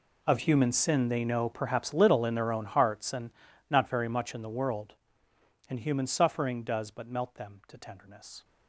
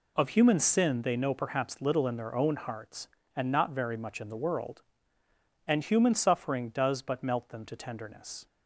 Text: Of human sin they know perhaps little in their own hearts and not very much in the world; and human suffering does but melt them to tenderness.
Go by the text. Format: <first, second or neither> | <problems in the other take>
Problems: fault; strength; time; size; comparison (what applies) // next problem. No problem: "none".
second | gets quieter; strong; throughout; 19.5 dB // pauses between "and" and "not"; at 3.3 s; 0.38 s long